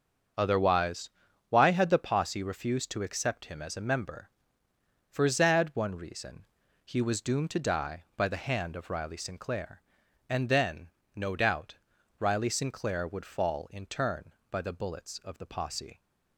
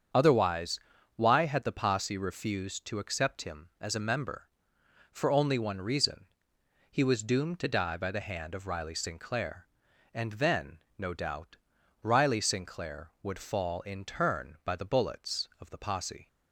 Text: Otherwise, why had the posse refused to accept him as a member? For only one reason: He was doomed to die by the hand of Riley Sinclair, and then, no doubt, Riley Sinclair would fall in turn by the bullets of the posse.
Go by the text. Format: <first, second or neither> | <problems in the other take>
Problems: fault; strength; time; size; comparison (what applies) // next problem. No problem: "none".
second | starts louder than the rest; until 1.7 s; 6.5 dB; strong in the second // says "zad" for "only"; at 5.2 s